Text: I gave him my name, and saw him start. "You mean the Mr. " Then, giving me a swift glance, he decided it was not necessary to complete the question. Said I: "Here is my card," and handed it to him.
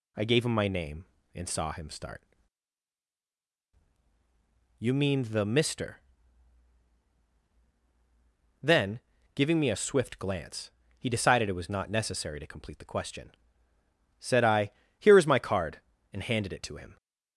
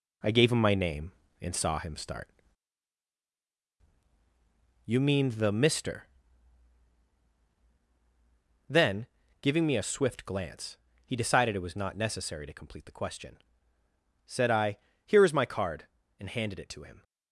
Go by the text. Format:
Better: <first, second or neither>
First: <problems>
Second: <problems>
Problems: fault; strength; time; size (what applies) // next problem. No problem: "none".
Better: first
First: none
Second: gets quieter; noticeable; throughout; 4 dB